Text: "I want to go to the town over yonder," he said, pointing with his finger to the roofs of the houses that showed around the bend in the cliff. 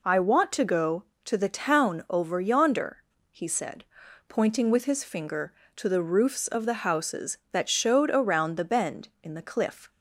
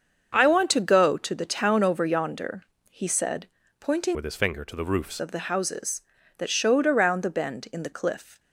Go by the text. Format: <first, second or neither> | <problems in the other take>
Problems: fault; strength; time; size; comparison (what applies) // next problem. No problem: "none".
first | starts louder than the rest; until 1.3 s; 7 dB // changes voice from "with" to "roofs"; from 4.1 to 5.2 s; 1.1 s long